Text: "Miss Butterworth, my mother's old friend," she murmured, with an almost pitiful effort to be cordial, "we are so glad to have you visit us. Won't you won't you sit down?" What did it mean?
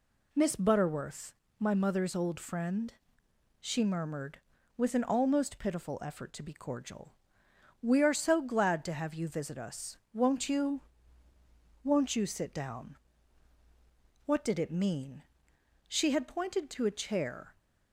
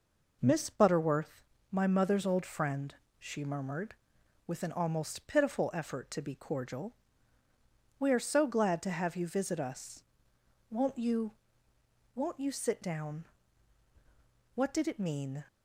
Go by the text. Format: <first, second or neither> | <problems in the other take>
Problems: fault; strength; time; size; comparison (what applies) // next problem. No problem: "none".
second | pauses between "you" and "won't"; at 10.8 s; 1.0 s long; noticeable in the second // goes on to say "She had pointed to a chair"; from 15.8 s on; 1.6 s long